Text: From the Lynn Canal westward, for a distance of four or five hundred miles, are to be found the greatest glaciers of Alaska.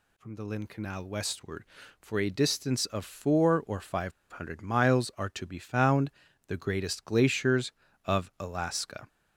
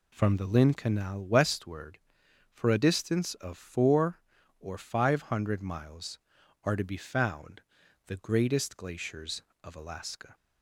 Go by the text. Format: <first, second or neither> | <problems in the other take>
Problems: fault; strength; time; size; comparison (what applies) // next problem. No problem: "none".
second | pauses between "five" and "hundred"; slight; at 4.1 s; 0.21 s long // pauses between "found" and "the"; at 6.1 s; 0.38 s long; noticeable in the second